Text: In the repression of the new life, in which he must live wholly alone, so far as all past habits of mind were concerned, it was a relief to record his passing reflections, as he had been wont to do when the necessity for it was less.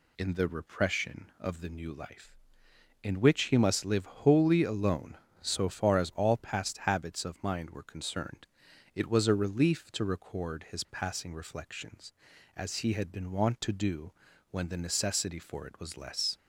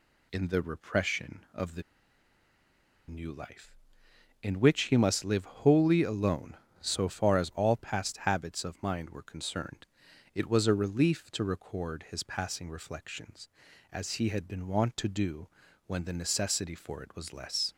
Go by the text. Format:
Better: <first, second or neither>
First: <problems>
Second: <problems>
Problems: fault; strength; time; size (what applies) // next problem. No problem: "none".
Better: first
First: pauses between "do" and "when"; at 14.1 s; 0.40 s long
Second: pauses between "the" and "new"; strong; at 1.8 s; 1.2 s long // pauses between "do" and "when"; at 15.4 s; 0.40 s long